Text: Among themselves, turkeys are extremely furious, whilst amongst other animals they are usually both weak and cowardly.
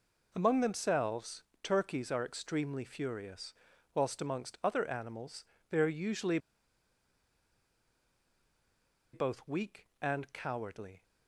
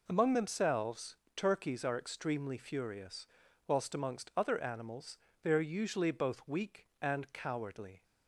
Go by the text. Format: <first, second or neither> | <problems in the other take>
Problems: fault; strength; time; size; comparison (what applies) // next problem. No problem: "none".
second | pauses between "animals" and "they"; slight; at 5.4 s; 0.26 s long; slight in the second // pauses between "usually" and "both"; strong; at 6.3 s; 2.7 s long